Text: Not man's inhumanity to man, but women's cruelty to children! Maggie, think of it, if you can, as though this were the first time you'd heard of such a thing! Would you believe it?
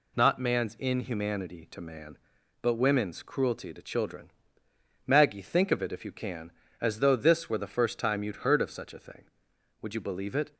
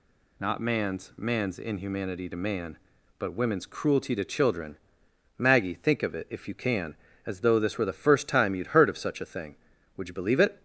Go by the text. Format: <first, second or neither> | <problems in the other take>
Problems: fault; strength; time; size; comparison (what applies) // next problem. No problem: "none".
first | says "man's" twice; at 1.1 s